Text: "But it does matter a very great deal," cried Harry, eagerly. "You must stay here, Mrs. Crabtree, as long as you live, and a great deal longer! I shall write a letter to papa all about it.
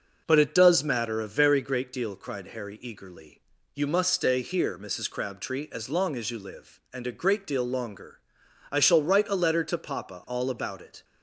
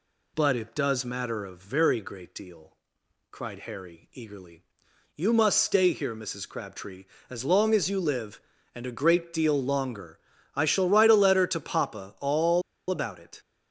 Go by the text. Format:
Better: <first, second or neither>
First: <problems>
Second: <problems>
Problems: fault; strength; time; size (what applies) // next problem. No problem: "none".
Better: first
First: none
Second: pauses between "all" and "about"; slight; at 12.6 s; 0.28 s long